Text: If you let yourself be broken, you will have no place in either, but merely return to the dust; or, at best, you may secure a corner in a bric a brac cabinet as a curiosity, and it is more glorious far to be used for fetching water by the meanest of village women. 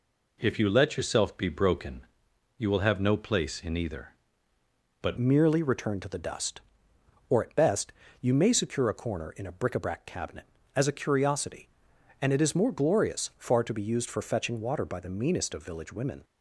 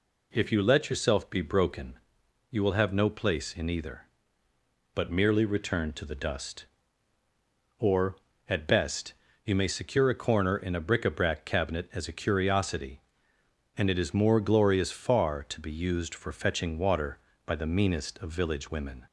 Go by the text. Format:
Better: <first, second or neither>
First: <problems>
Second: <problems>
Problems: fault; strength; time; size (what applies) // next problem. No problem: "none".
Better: second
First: changes voice at "merely"; from 5.1 s on; 11.1 s long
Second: none